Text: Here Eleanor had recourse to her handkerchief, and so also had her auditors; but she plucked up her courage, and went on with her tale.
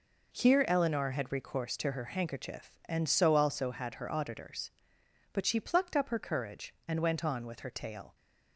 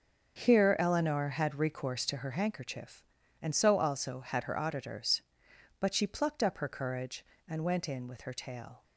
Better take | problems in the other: first | starts louder than the rest; until 1.4 s; 6.5 dB // says "in" for "on"; at 7.8 s

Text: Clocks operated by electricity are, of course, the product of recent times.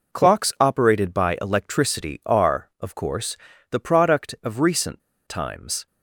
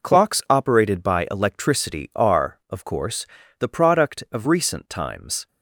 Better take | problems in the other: second | pauses between "recent" and "times"; slight; at 5.0 s; 0.27 s long

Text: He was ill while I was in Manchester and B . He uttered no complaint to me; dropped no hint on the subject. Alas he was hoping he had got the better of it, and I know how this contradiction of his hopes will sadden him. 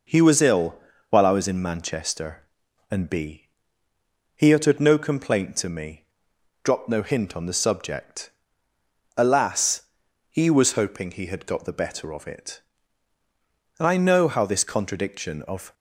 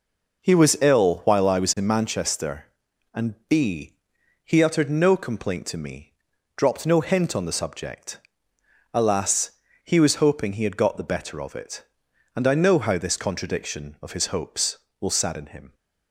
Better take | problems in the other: second | pauses between "ill" and "while"; slight; at 0.7 s; 0.36 s long // pauses between "Alas" and "he"; noticeable; at 9.8 s; 0.48 s long; slight in the second // stops before "his hopes will sadden him"; at 15.7 s

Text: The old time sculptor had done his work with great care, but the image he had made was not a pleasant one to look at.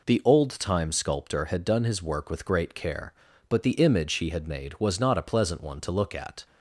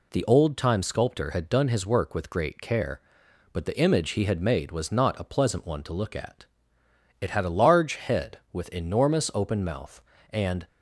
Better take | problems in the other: first | goes on to say "It had a large head with enormous open mouth and"; strong; from 7.1 s on; 3.4 s long

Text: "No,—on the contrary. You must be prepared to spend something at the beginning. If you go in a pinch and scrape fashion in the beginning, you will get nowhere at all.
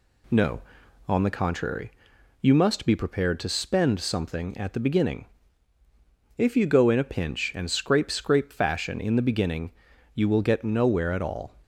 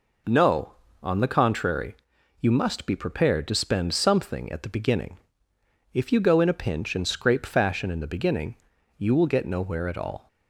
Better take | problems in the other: second | says "scrape" twice; at 8.1 s

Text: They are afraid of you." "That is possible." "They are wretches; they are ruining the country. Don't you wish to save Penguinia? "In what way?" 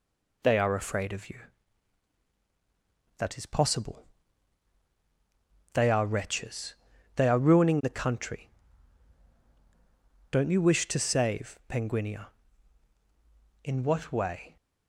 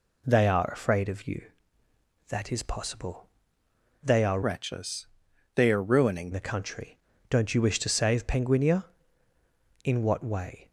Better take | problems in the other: first | changes voice from "wretches" to "ruining"; from 4.4 to 6.3 s; 1.9 s long

